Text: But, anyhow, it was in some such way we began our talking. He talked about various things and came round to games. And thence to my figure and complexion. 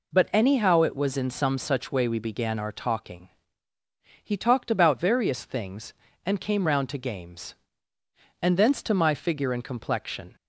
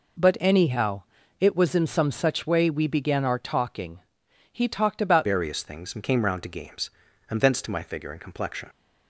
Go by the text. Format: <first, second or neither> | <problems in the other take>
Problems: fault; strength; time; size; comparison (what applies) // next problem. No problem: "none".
first | changes voice at "various"; from 5.2 s on; 3.4 s long